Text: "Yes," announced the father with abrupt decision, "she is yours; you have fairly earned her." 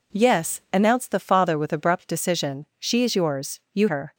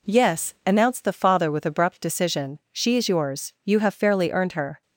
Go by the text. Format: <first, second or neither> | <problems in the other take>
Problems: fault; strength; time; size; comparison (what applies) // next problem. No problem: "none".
second | skips "have fairly earned"; at 3.8 s